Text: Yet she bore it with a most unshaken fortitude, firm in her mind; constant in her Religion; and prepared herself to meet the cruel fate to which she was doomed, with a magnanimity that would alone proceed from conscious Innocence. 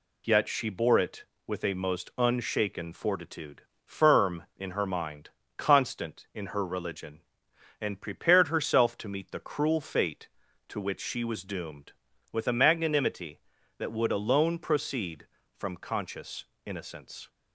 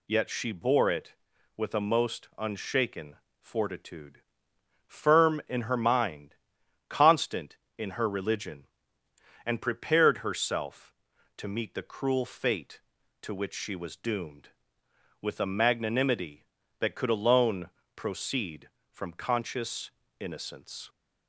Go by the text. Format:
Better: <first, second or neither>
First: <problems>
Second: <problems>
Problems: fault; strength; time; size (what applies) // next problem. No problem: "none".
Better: first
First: pauses between "conscious" and "Innocence"; slight; at 16.4 s; 0.20 s long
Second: pauses between "unshaken" and "fortitude"; slight; at 3.1 s; 0.26 s long // says "could" for "would"; at 16.9 s // pauses between "alone" and "proceed"; slight; at 17.6 s; 0.26 s long // pauses between "conscious" and "Innocence"; slight; at 19.9 s; 0.30 s long